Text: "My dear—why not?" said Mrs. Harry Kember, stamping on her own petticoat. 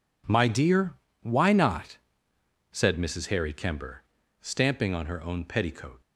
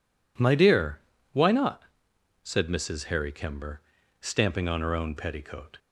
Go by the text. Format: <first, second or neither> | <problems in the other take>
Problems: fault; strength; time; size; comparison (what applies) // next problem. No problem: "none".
neither | none